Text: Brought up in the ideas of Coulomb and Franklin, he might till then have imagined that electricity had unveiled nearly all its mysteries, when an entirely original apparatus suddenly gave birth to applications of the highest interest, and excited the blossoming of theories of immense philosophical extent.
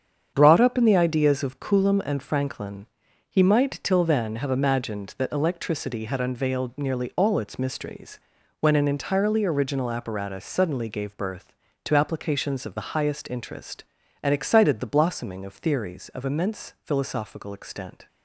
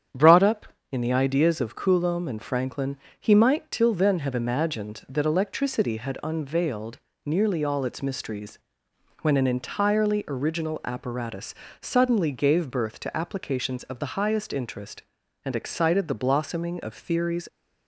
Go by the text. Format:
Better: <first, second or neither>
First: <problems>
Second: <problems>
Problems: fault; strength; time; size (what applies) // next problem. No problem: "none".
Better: first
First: starts louder than the rest; strong; until 1.3 s; 8 dB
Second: starts louder than the rest; strong; until 1.3 s; 8.5 dB // pauses between "unveiled" and "nearly"; slight; at 6.9 s; 0.26 s long // pauses between "apparatus" and "suddenly"; slight; at 11.5 s; 0.26 s long // stops before "of immense philosophical extent"; at 17.4 s